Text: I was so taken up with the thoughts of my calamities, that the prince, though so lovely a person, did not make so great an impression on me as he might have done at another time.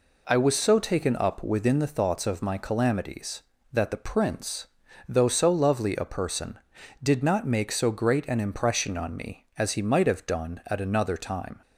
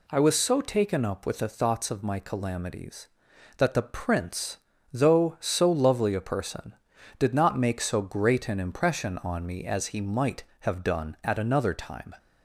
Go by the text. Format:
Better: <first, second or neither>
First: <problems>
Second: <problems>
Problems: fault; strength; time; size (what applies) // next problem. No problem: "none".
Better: second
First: says "within" for "with"; at 1.4 s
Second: none